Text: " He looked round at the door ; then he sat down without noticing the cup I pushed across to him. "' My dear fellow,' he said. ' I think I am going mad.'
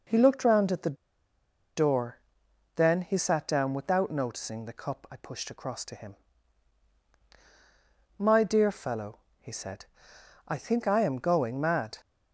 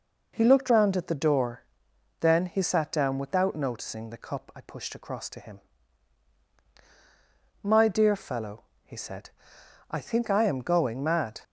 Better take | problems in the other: second | starts louder than the rest; until 1.8 s; 6.5 dB; also in the second // pauses between "the" and "door"; noticeable; at 0.9 s; 0.80 s long

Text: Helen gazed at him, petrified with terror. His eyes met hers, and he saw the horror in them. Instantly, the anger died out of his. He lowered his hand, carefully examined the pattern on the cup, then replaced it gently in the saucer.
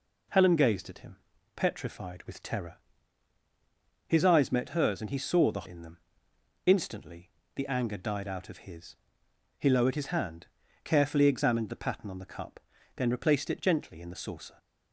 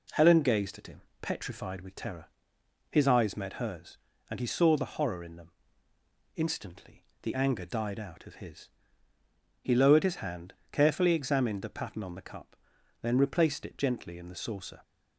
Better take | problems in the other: second | skips "horror"; at 5.6 s

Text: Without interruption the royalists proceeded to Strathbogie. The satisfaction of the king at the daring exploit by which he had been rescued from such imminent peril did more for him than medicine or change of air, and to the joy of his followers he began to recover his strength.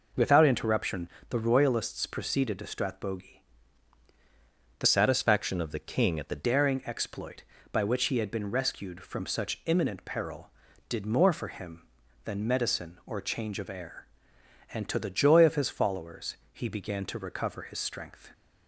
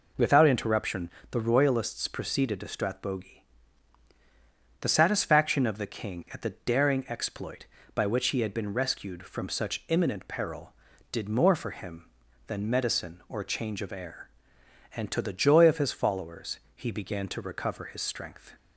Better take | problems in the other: second | pauses between "interruption" and "the"; slight; at 1.0 s; 0.22 s long; slight in the second // changes voice from "satisfaction" to "the"; from 4.8 to 6.4 s; 1.6 s long // pauses between "followers" and "he"; slight; at 16.3 s; 0.16 s long; slight in the second

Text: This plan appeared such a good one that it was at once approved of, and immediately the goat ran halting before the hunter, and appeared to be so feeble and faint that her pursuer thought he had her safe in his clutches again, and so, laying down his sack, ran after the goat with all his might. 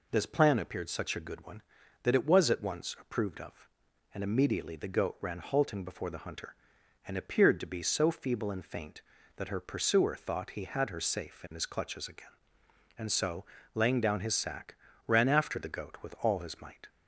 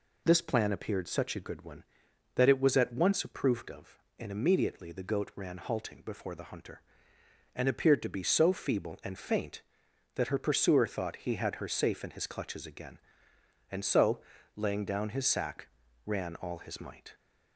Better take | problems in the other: first | skips "after the goat with"; at 16.3 s

